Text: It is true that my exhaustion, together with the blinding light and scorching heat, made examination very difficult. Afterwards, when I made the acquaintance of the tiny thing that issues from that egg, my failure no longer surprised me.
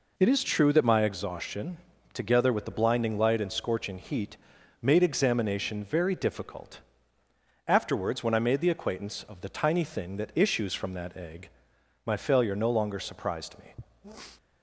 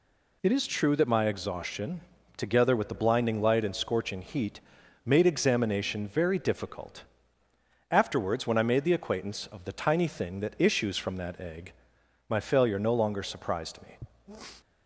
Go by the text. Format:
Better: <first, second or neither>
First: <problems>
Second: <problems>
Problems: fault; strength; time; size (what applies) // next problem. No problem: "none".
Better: second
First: starts louder than the rest; noticeable; until 1.2 s; 4 dB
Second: none